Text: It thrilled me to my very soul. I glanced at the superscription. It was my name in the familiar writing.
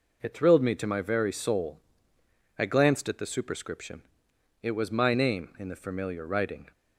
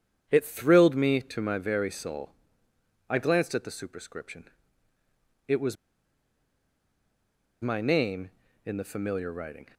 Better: first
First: none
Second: starts louder than the rest; strong; until 1.3 s; 8.5 dB // pauses between "was" and "my"; strong; at 5.7 s; 1.8 s long

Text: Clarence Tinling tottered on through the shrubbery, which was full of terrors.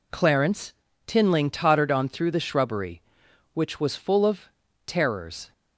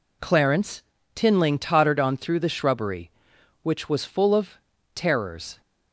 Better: neither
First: pauses between "Clarence" and "Tinling"; slight; at 0.7 s; 0.34 s long // pauses between "of" and "terrors"; slight; at 4.4 s; 0.36 s long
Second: pauses between "Clarence" and "Tinling"; slight; at 0.8 s; 0.33 s long // pauses between "of" and "terrors"; slight; at 4.5 s; 0.35 s long

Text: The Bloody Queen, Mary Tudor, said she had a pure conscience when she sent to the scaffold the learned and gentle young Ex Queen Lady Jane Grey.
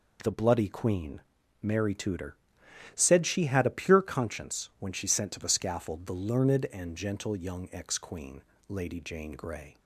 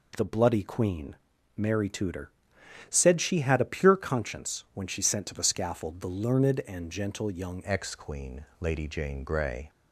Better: first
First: pauses between "Queen" and "Lady"; slight; at 8.4 s; 0.26 s long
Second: changes voice at "Ex"; from 7.6 s on; 2.0 s long // pauses between "Queen" and "Lady"; slight; at 8.4 s; 0.16 s long

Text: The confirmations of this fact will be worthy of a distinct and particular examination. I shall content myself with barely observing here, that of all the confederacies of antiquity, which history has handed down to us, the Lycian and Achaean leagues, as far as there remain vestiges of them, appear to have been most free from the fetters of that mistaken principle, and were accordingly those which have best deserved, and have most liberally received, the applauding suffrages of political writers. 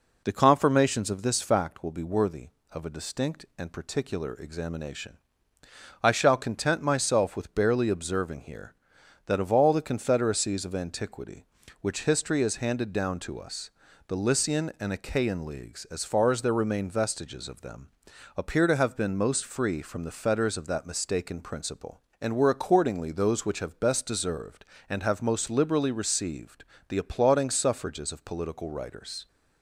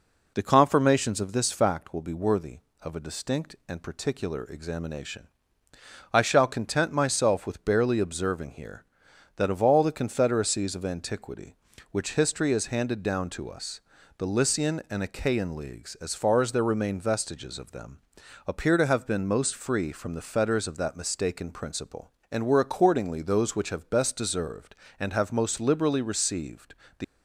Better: first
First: none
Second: stops before "applauding suffrages of political writers"; at 27.0 s

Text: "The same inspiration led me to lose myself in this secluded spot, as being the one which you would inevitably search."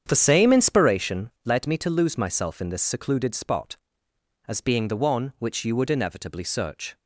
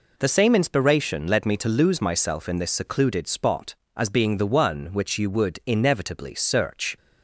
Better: second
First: starts louder than the rest; strong; until 1.0 s; 8 dB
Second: none

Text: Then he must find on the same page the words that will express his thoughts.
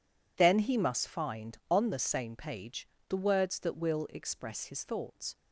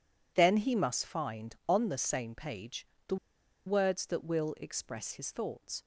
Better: first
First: pauses between "page" and "the"; slight; at 2.8 s; 0.22 s long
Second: pauses between "page" and "the"; slight; at 2.8 s; 0.22 s long // pauses between "the" and "words"; noticeable; at 3.1 s; 0.50 s long

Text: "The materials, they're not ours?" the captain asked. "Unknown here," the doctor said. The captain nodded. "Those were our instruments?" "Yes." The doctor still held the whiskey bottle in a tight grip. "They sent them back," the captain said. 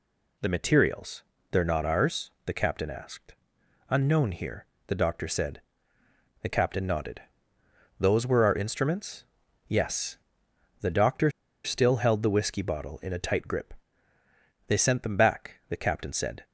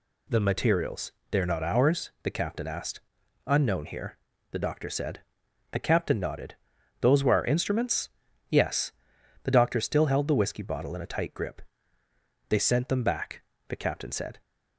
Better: second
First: pauses between "doctor" and "still"; slight; at 11.3 s; 0.33 s long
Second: none

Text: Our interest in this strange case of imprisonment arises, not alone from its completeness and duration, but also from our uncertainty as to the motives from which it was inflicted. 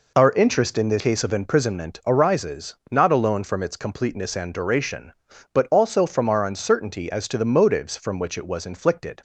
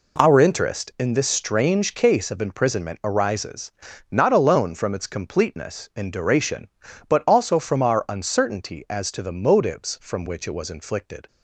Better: second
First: skips "strange"; at 1.0 s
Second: none

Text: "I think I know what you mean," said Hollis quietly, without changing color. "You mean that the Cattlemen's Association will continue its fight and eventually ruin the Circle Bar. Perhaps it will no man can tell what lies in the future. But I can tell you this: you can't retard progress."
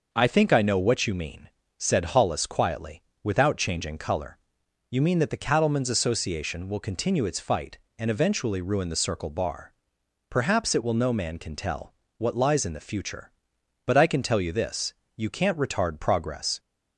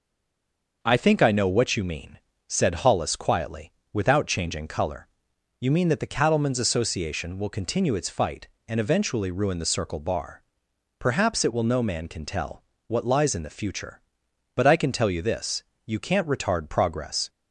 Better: first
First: starts louder than the rest; noticeable; until 1.1 s; 6 dB // pauses between "tell" and "what"; slight; at 11.9 s; 0.24 s long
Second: stays silent before the first word; slight; until 0.8 s; 0.8 s long // starts louder than the rest; noticeable; until 1.8 s; 6 dB // pauses between "tell" and "what"; slight; at 12.6 s; 0.24 s long

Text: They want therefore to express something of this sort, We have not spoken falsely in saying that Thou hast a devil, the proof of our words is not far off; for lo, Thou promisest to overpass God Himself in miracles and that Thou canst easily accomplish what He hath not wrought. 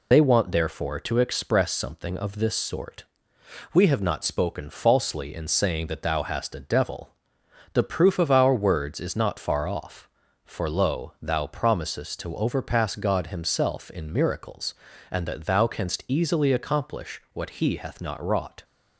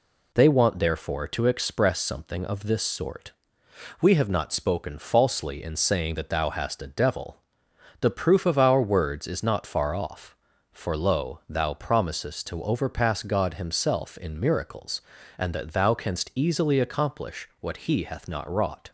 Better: second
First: loses the start of "They"; at 0.1 s; 45 ms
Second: none

